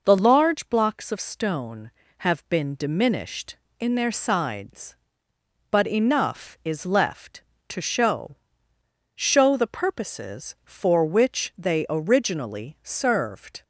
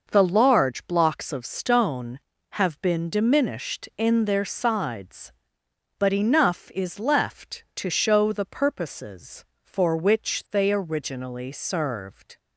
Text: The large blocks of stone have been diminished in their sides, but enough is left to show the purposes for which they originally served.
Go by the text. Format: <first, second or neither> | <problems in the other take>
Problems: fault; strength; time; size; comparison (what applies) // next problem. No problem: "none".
second | says "show" twice; at 9.1 s